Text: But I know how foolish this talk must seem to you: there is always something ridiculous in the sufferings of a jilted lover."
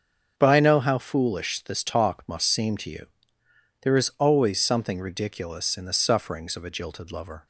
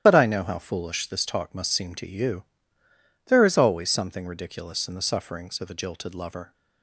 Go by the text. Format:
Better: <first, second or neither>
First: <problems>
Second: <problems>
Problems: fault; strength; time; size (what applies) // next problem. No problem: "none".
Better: first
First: starts louder than the rest; strong; until 1.3 s; 7.5 dB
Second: loses the start of "But"; at 0.0 s; 35 ms // starts louder than the rest; strong; until 1.0 s; 11 dB